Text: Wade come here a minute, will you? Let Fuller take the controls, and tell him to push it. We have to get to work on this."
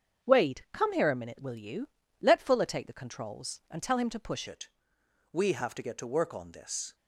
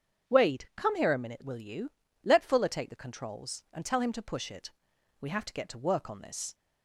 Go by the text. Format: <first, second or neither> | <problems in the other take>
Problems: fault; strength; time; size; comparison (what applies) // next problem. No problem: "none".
second | starts louder than the rest; strong; until 1.3 s; 7.5 dB; strong in the second // changes voice at "it"; from 4.4 s on; 2.5 s long